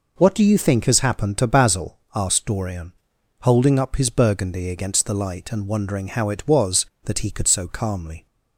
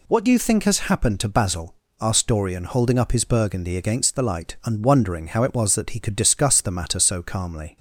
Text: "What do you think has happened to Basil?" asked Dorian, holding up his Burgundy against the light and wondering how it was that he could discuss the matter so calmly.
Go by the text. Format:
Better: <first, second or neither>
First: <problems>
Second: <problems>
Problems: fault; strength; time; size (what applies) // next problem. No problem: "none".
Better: second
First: skips "discuss the matter"; at 7.4 s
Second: none